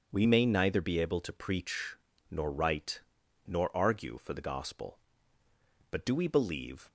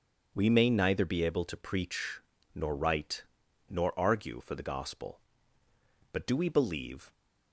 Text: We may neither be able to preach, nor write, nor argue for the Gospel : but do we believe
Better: neither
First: starts louder than the rest; until 1.1 s; 7 dB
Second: starts louder than the rest; until 1.3 s; 6.5 dB

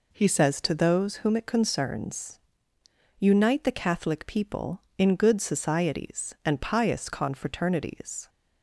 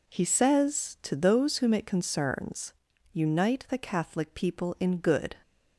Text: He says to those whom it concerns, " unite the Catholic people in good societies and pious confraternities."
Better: first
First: none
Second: stops before "societies and pious confraternities"; at 5.4 s

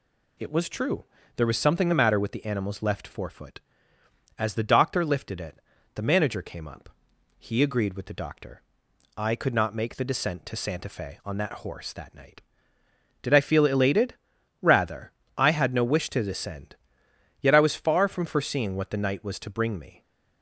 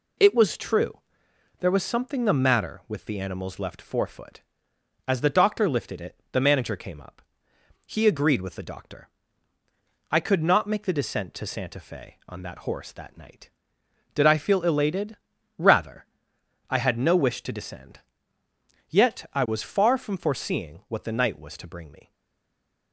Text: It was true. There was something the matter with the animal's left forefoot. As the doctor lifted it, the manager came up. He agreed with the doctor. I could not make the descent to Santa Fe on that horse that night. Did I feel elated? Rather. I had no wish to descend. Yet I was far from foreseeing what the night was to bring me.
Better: first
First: none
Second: stays silent after the last word; slight; from 22.1 s on; 0.8 s long

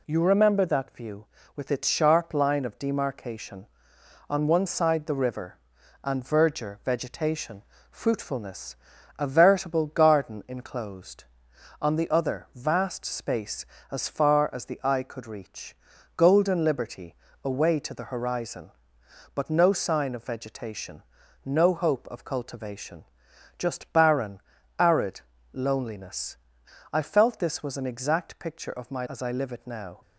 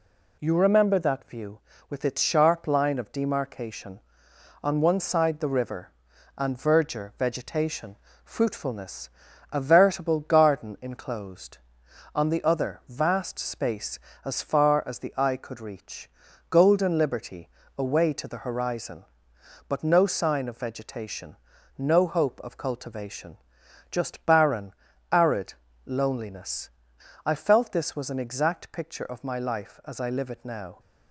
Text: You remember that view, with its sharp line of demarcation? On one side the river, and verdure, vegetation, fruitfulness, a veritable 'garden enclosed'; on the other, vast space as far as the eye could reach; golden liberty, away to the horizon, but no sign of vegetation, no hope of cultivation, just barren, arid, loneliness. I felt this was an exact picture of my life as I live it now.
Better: second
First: skips "life"; at 29.0 s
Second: none

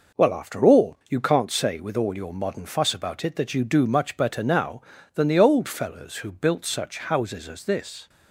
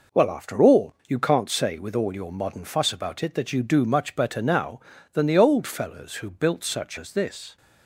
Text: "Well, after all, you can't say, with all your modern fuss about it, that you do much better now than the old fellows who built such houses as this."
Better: first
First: none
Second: skips "houses"; at 6.9 s

